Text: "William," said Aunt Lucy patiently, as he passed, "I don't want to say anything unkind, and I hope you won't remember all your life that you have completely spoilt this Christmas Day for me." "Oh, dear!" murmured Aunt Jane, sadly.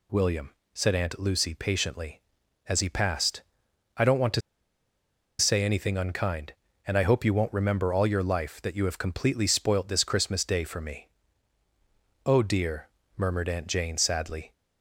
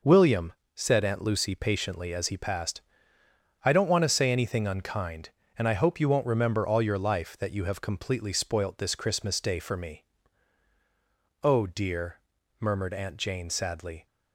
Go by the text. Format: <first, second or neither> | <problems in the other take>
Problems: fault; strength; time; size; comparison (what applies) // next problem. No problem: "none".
second | pauses between "to" and "say"; at 4.4 s; 0.98 s long